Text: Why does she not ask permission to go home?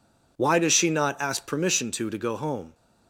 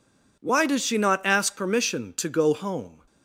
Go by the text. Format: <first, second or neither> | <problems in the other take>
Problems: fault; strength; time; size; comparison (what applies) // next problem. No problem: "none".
second | says "to" twice; at 2.0 s